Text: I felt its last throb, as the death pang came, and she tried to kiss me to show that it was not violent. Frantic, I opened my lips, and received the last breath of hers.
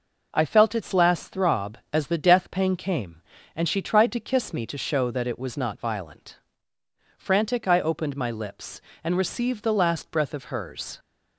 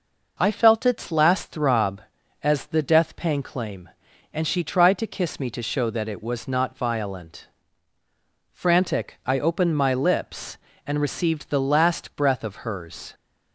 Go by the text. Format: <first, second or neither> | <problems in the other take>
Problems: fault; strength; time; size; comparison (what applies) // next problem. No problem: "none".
first | says "claim" for "came"; at 3.4 s